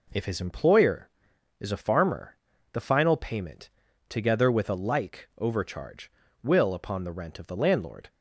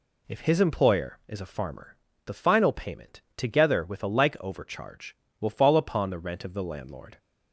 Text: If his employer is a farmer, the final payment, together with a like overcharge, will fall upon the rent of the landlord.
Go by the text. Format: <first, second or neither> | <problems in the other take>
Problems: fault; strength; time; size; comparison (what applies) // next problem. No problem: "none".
second | skips "fall"; at 6.7 s